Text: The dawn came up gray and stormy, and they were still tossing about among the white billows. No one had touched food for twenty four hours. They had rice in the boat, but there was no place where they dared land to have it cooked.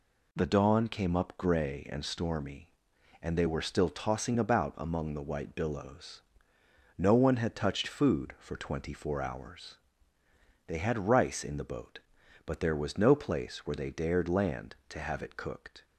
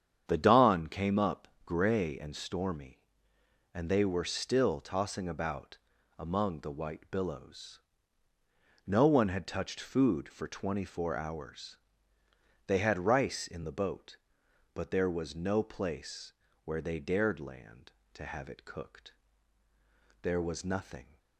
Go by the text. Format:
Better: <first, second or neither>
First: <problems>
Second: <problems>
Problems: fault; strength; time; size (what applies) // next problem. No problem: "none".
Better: first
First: none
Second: starts louder than the rest; strong; until 1.2 s; 8.5 dB // pauses between "up" and "gray"; slight; at 1.4 s; 0.18 s long // pauses between "about" and "among"; at 5.7 s; 0.40 s long // pauses between "place" and "where"; slight; at 16.3 s; 0.32 s long // goes on to say "There was nothing"; noticeable; from 20.2 s on; 0.94 s long